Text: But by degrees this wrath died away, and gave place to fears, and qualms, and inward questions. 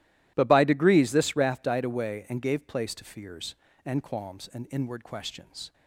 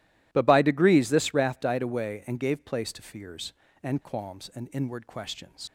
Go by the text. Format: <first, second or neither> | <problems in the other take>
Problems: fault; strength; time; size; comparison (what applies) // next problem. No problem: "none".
first | leaves "questions" unfinished; at 5.6 s; 90 ms